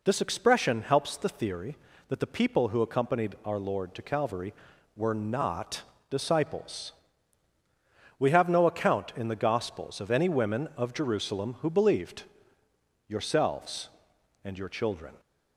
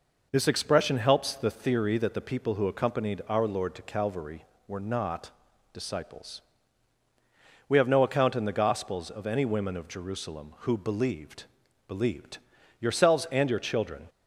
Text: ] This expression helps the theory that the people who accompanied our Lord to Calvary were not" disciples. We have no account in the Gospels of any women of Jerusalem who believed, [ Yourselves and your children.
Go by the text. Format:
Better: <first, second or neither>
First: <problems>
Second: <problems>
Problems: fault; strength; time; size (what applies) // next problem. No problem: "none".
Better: first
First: pauses between "not" and "disciples"; slight; at 5.8 s; 0.26 s long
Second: pauses between "not" and "disciples"; at 5.3 s; 0.42 s long // says "believed" twice; at 11.8 s